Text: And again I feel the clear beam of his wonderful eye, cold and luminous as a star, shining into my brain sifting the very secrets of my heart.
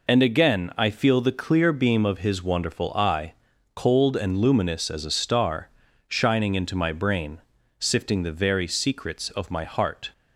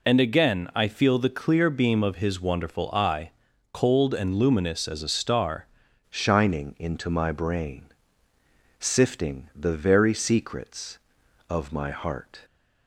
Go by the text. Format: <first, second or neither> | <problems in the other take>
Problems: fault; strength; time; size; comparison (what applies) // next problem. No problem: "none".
first | changes voice at "shining"; from 6.1 s on; 6.3 s long // pauses between "brain" and "sifting"; noticeable; at 7.8 s; 0.98 s long; also in the first